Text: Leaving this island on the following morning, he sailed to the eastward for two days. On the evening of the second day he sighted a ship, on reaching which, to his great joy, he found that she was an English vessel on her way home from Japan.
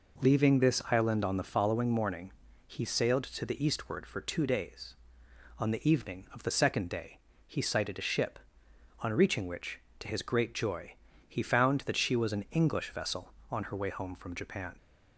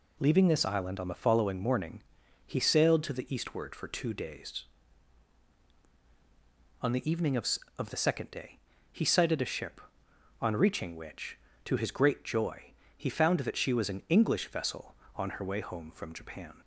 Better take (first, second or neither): first